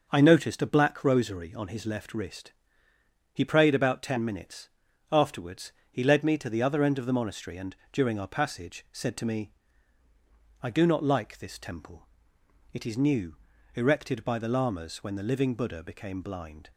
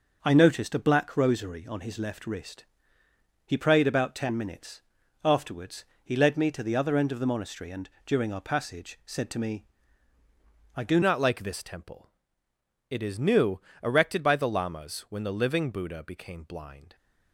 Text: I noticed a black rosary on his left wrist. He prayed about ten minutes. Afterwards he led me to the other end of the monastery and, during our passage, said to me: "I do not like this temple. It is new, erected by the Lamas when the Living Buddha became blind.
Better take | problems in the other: first | starts louder than the rest; until 1.2 s; 6 dB; noticeable in the first // pauses between "Afterwards" and "he"; slight; at 5.8 s; 0.20 s long; slight in the first // changes voice at "not"; from 11.0 s on; 5.9 s long

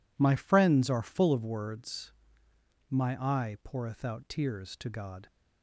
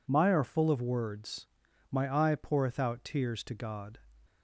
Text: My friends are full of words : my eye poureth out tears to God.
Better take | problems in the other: first | skips "friends"; at 0.3 s

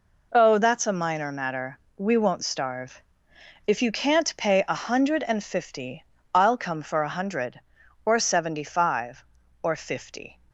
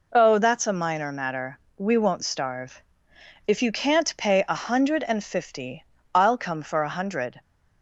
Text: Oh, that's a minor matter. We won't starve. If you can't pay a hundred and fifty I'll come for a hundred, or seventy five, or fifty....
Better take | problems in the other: first | pauses between "fifty" and "I'll"; slight; at 5.8 s; 0.32 s long; slight in the first // stops before "or seventy five or fifty"; at 7.4 s

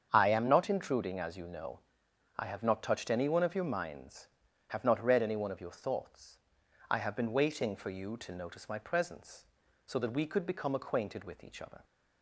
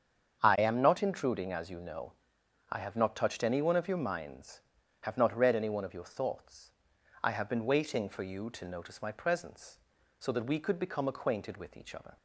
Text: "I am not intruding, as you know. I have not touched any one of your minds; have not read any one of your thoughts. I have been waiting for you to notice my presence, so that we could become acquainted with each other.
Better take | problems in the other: neither | starts louder than the rest; strong; the same in both

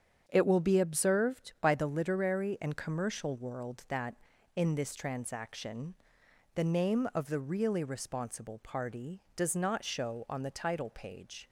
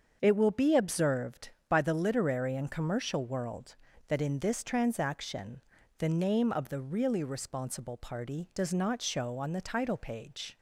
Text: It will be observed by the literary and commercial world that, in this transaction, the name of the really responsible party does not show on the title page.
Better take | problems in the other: neither | starts louder than the rest; the same in both

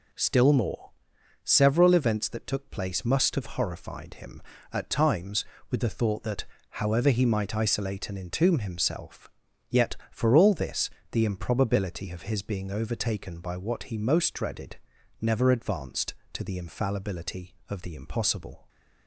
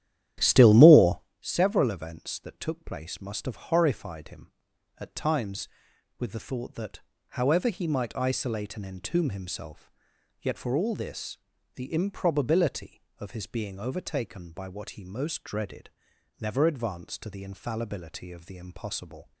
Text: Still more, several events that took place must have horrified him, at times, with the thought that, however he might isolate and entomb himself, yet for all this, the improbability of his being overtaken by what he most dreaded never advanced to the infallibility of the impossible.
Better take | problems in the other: first | starts louder than the rest; strong; until 1.3 s; 11.5 dB // pauses between "dreaded" and "never"; noticeable; at 15.8 s; 0.52 s long; also in the first

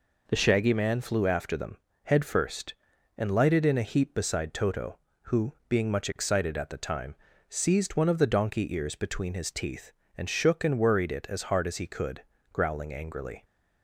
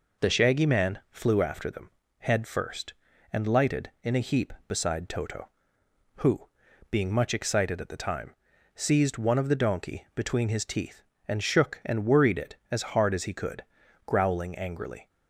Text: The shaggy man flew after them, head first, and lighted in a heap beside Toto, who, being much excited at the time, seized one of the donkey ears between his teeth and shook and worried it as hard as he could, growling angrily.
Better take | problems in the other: first | skips "ears"; at 10.1 s

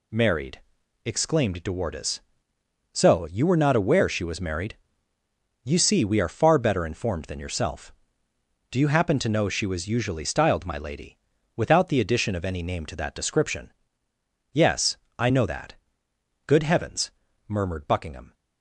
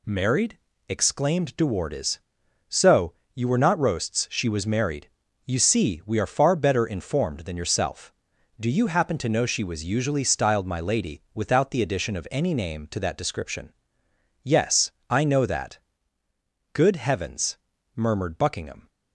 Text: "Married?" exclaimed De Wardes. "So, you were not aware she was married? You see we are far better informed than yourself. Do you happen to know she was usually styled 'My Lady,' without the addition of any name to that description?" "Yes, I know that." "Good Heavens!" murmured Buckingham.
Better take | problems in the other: first | says "roasts" for "aware"; at 3.7 s

